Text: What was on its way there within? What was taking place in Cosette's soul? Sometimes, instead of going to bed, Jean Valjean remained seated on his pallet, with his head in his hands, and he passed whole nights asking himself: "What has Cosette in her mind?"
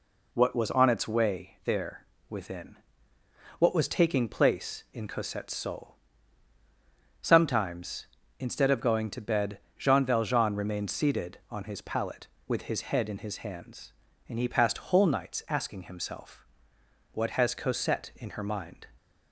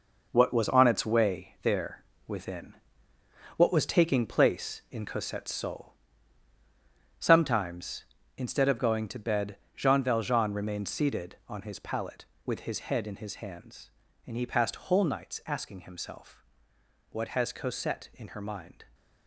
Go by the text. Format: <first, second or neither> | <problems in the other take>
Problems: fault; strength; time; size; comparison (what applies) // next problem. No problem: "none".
first | gets quieter; strong; throughout; 8.5 dB // pauses between "there" and "within"; slight; at 2.0 s; 0.24 s long; slight in the first